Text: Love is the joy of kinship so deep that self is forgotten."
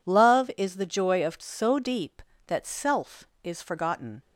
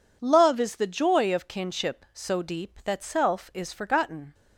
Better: second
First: skips "kinship"; at 1.3 s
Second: none

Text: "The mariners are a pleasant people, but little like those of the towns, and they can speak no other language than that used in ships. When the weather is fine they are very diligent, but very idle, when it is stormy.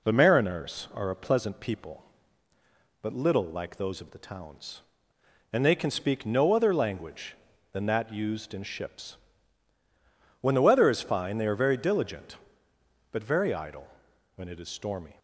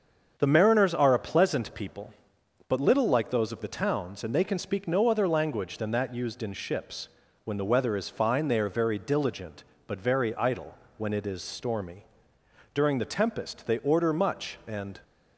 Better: first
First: none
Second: starts louder than the rest; until 1.3 s; 7 dB // goes on to say "During the tempest they order much and"; strong; from 12.7 s on; 2.2 s long

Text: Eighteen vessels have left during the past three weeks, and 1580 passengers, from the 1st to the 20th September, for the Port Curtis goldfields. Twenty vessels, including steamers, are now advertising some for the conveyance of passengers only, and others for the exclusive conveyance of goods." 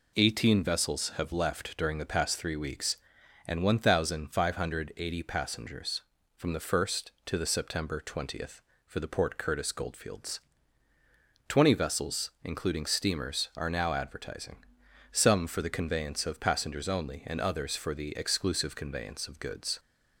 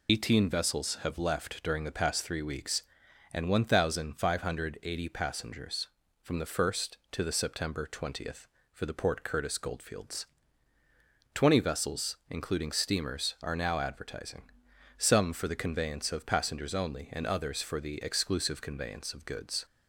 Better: first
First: pauses between "advertising" and "some"; noticeable; at 14.5 s; 0.54 s long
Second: loses the start of "Eighteen"; at 0.0 s; 85 ms // pauses between "advertising" and "some"; noticeable; at 14.4 s; 0.54 s long

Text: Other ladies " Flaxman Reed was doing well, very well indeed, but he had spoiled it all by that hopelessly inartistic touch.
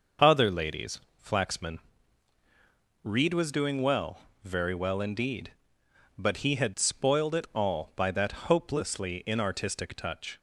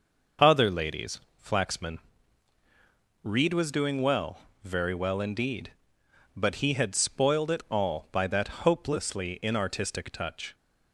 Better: neither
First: pauses between "Flaxman" and "Reed"; at 1.7 s; 1.2 s long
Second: pauses between "Flaxman" and "Reed"; at 1.9 s; 1.2 s long

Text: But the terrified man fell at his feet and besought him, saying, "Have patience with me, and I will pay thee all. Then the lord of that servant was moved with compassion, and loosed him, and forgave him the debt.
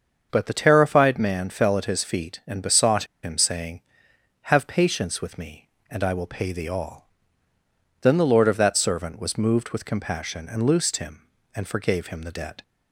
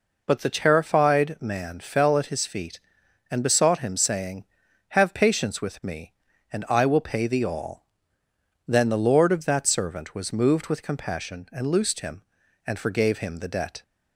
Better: second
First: starts louder than the rest; until 1.3 s; 6.5 dB // pauses between "besought" and "him"; slight; at 3.0 s; 0.19 s long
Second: none

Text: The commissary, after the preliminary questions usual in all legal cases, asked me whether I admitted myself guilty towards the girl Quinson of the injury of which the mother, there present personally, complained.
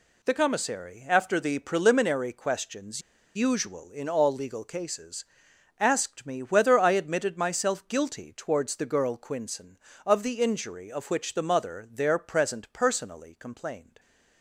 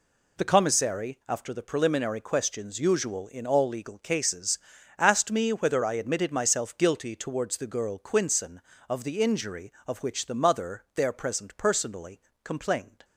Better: second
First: pauses between "questions" and "usual"; slight; at 3.0 s; 0.34 s long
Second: none

